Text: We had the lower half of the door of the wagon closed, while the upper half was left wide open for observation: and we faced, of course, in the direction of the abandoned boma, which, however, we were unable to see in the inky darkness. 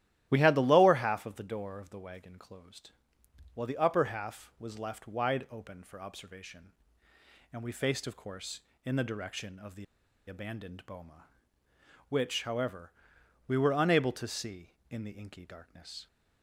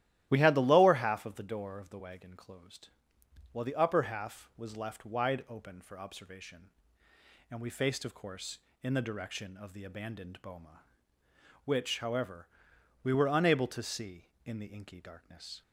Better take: second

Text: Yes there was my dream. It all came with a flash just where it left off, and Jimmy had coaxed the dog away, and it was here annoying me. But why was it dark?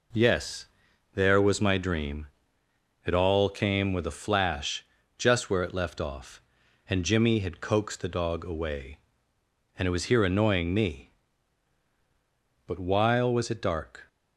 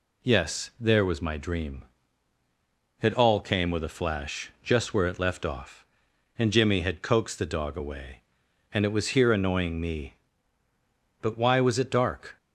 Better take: second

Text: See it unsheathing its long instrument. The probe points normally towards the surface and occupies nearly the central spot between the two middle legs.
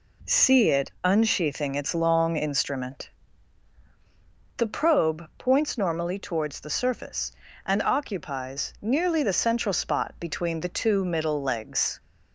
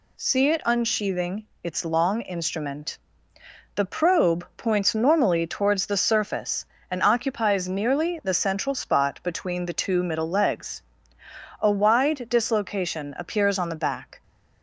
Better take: first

